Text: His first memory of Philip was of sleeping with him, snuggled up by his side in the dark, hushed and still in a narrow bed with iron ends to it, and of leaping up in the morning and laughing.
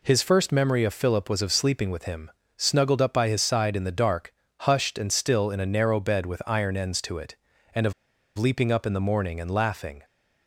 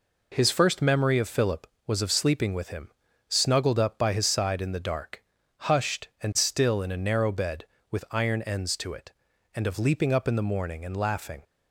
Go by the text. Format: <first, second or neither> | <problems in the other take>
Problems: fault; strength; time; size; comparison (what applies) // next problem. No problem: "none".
second | pauses between "of" and "leaping"; at 7.9 s; 0.44 s long